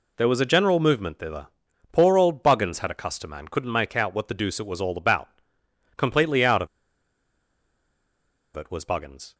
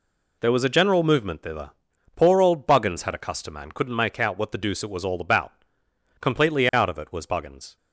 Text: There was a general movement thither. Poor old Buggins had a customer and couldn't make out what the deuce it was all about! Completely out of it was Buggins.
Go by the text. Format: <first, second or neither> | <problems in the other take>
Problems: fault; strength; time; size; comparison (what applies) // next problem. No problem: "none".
second | pauses between "of" and "it"; strong; at 6.6 s; 1.8 s long